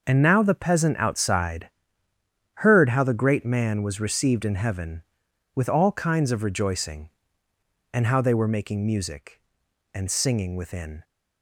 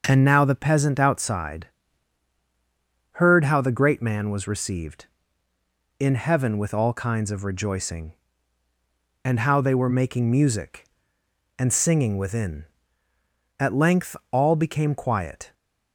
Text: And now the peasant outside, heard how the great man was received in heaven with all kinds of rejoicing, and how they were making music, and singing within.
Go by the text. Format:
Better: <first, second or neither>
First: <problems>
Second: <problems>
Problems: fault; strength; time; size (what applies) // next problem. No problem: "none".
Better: first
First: none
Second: starts louder than the rest; until 1.0 s; 6 dB // goes on to say "At length all became quiet"; strong; from 13.5 s on; 1.9 s long